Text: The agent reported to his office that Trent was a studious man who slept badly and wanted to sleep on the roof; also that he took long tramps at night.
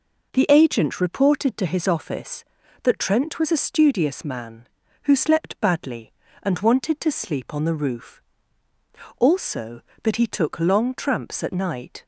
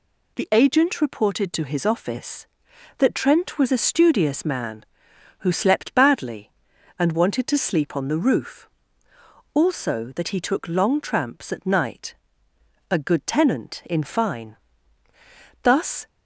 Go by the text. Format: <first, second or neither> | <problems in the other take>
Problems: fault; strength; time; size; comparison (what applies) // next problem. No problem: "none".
first | goes on to say "A good tenant in fine Thus"; strong; from 12.9 s on; 3.1 s long